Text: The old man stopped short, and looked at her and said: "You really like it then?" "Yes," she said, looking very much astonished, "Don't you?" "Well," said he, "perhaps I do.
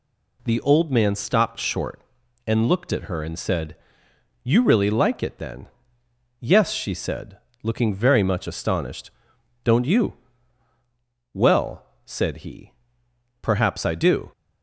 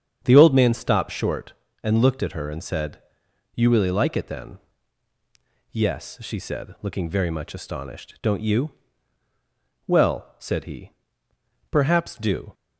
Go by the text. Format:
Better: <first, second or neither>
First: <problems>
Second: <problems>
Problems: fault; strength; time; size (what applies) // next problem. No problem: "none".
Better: first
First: none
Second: starts louder than the rest; strong; until 1.2 s; 7.5 dB // skips "I"; at 12.1 s